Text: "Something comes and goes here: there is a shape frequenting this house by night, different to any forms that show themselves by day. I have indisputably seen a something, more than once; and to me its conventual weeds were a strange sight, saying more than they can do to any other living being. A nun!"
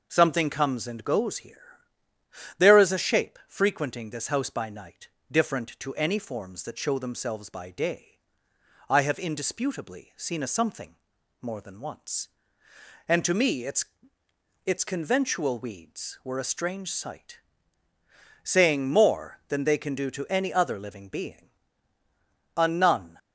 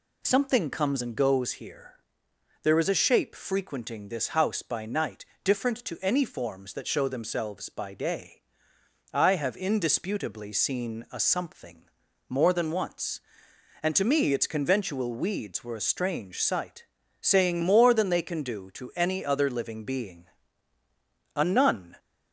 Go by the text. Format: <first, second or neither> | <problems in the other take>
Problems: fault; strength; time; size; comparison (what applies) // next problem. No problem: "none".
second | says "its" twice; at 14.6 s